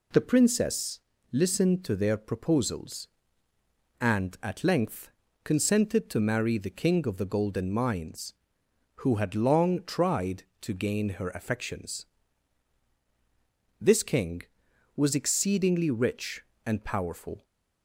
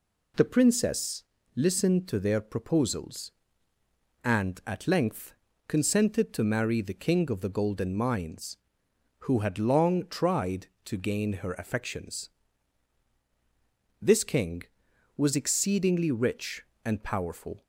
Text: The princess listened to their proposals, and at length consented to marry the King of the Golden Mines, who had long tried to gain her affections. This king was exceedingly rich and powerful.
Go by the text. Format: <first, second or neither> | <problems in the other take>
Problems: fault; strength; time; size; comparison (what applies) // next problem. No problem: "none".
neither | pauses between "princess" and "listened"; slight; the same in both // pauses between "length" and "consented"; slight; the same in both